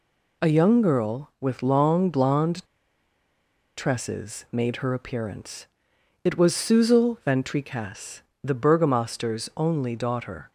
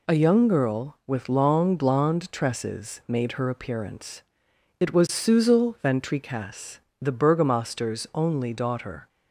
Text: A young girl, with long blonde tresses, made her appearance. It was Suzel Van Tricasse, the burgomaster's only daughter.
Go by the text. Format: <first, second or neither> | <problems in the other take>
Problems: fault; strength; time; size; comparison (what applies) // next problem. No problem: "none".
second | pauses between "blonde" and "tresses"; at 2.6 s; 1.1 s long